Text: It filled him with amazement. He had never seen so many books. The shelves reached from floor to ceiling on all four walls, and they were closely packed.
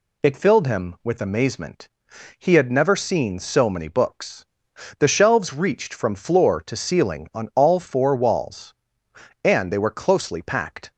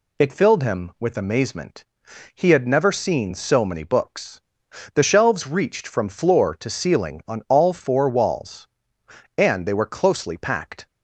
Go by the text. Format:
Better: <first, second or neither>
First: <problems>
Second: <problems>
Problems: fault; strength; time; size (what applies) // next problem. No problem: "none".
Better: neither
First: none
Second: none